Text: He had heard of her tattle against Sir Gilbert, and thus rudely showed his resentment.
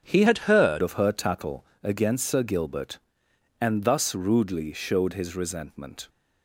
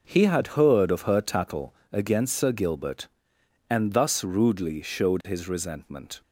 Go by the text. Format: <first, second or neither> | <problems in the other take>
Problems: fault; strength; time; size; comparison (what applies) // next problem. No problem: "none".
second | starts louder than the rest; until 1.0 s; 7 dB // changes voice from "had" to "heard"; from 0.2 to 0.8 s; 0.6 s long // pauses between "tattle" and "against"; slight; at 1.6 s; 0.18 s long; slight in the second